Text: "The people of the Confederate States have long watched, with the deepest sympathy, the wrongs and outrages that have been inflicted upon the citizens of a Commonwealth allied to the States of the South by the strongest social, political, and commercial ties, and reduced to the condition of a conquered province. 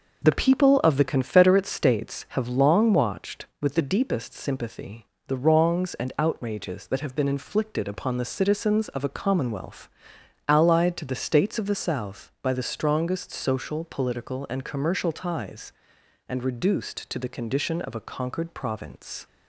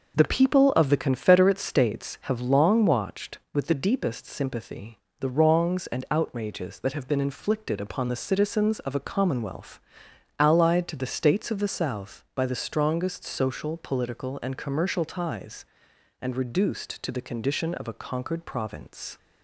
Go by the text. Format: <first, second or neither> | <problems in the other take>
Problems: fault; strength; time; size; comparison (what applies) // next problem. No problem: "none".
neither | pauses between "Commonwealth" and "allied"; noticeable; the same in both